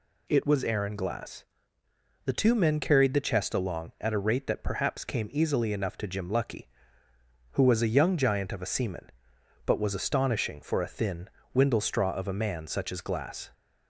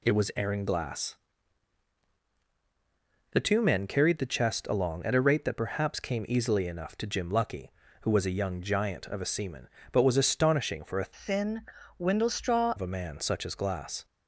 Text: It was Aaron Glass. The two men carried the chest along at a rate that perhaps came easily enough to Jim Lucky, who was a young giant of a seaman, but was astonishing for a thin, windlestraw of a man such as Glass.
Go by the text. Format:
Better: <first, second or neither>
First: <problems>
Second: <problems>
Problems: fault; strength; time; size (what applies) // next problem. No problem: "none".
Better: first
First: none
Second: changes voice from "thin" to "windlestraw"; from 11.1 to 12.7 s; 1.6 s long